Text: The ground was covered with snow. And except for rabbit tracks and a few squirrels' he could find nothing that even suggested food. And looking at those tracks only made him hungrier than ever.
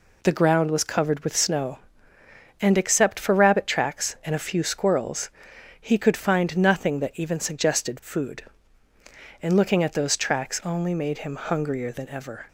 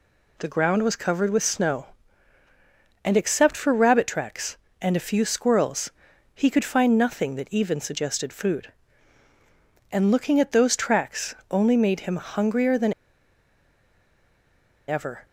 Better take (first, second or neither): first